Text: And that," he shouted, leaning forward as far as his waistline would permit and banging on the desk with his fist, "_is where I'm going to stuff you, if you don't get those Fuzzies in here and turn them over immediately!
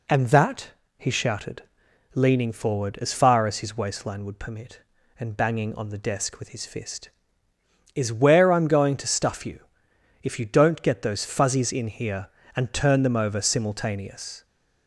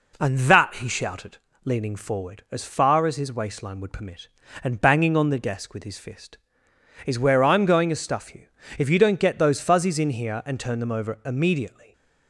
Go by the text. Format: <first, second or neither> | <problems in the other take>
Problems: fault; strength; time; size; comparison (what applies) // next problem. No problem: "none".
second | says "simultaneous" for "immediately"; at 13.4 s